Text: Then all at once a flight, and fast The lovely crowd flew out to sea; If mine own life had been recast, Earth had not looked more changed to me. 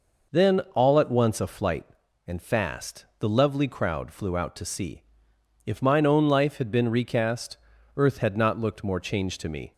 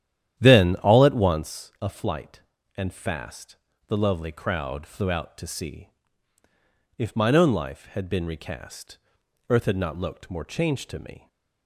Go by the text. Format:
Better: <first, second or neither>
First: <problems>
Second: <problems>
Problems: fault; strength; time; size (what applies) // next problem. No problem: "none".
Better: first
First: none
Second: starts louder than the rest; strong; until 1.6 s; 10.5 dB // pauses between "fast" and "The"; slight; at 3.5 s; 0.32 s long